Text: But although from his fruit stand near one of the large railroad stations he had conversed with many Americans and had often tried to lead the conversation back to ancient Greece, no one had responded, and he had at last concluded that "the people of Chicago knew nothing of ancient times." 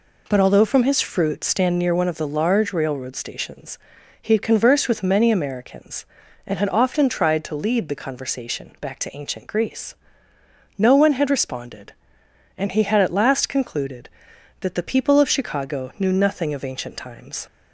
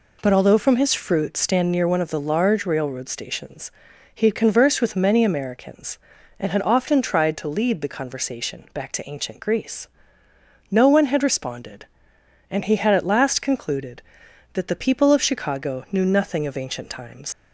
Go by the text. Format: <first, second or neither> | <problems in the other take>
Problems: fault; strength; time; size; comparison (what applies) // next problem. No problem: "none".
first | pauses between "stations" and "he"; at 3.7 s; 0.42 s long; also in the first // leaves "times" unfinished; at 17.3 s; 60 ms